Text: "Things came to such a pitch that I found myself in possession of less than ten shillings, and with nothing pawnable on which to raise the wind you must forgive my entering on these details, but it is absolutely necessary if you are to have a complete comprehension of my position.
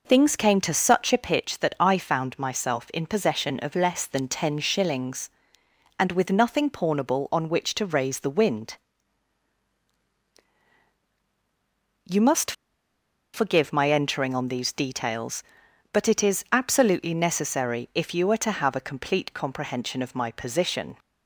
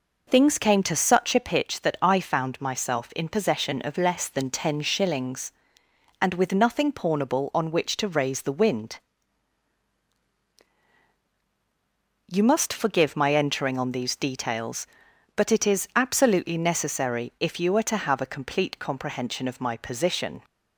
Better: second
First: pauses between "wind" and "you"; strong; at 8.7 s; 3.2 s long // pauses between "must" and "forgive"; noticeable; at 12.5 s; 0.81 s long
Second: pauses between "wind" and "you"; strong; at 9.0 s; 3.2 s long

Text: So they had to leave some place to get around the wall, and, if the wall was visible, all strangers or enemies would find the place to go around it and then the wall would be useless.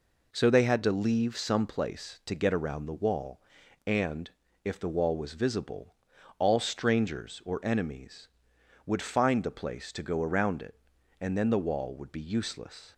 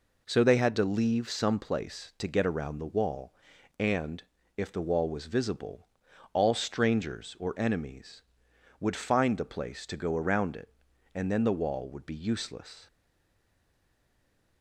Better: first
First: none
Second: stays silent after the last word; noticeable; from 12.8 s on; 1.8 s long

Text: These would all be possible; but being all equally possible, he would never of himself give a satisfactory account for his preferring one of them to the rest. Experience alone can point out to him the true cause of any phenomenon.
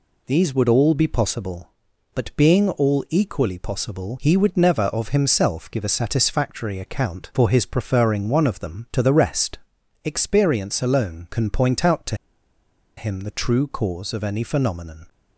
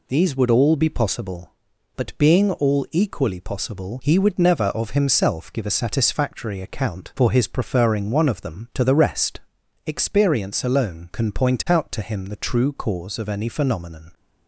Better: second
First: pauses between "to" and "him"; noticeable; at 12.1 s; 0.83 s long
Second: none

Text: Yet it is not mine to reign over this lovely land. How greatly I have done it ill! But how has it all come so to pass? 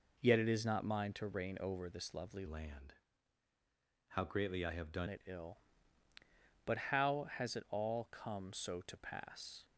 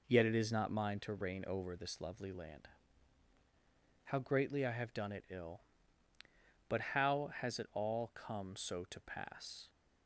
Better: second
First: changes voice from "land" to "done"; from 2.4 to 5.0 s; 2.6 s long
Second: none

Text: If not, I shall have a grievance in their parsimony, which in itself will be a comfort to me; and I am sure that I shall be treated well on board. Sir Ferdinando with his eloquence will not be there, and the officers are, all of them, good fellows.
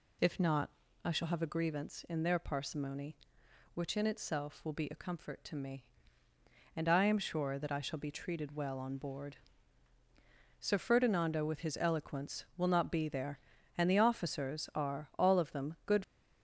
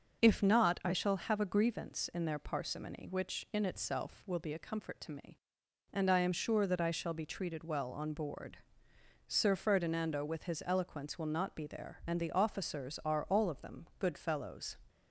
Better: second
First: stops before "fellows"; at 16.0 s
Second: none

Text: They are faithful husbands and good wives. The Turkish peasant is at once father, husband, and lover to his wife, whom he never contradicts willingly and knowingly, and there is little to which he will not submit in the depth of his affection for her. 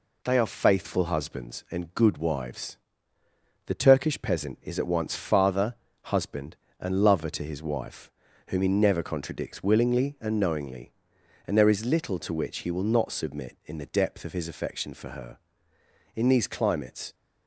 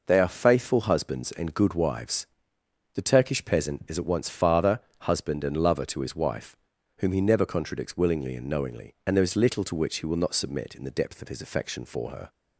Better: second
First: goes on to say "In these climates"; noticeable; from 16.1 s on; 1.0 s long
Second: none

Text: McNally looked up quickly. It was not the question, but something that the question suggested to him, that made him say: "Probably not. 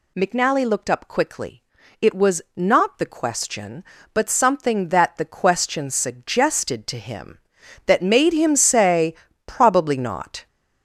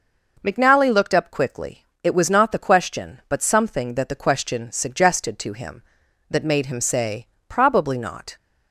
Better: second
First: gets louder; noticeable; throughout; 6 dB // pauses between "was" and "not"; slight; at 2.4 s; 0.16 s long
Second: none

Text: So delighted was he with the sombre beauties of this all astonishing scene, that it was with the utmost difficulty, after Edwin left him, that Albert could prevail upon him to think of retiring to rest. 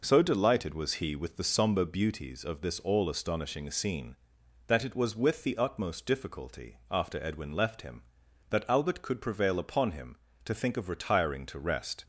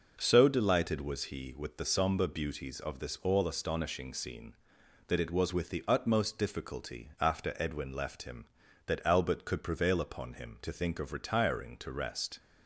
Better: neither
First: none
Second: none

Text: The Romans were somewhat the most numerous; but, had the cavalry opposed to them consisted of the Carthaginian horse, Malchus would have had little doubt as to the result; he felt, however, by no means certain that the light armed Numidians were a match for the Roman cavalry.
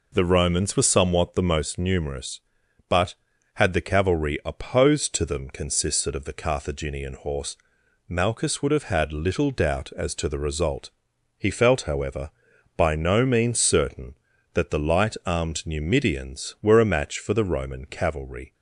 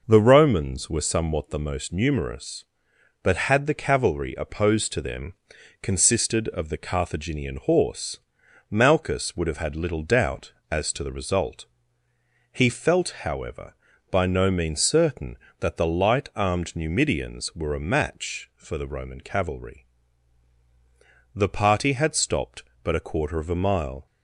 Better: first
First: none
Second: pauses between "them" and "consisted"; noticeable; at 5.3 s; 0.50 s long // goes on to say "The party had stopped but a quarter of a mile"; strong; from 21.3 s on; 2.7 s long

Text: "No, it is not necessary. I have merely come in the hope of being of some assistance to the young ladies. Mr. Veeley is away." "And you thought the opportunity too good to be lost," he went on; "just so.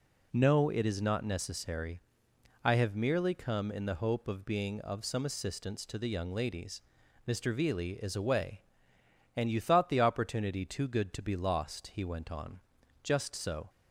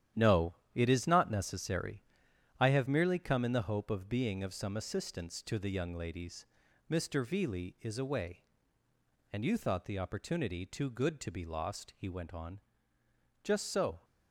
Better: first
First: none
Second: gets quieter; strong; throughout; 9 dB

